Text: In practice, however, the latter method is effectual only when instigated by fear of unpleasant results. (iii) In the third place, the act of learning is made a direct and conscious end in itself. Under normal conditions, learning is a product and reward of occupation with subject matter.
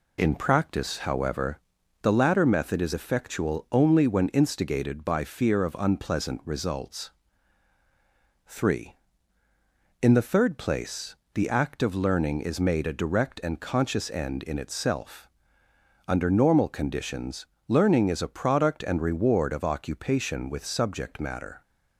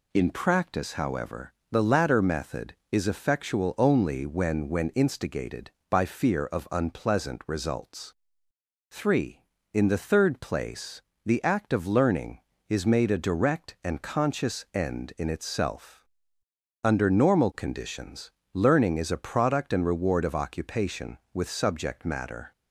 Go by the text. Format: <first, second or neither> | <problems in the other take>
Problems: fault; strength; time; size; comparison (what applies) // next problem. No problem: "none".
first | says "when" twice; at 4.6 s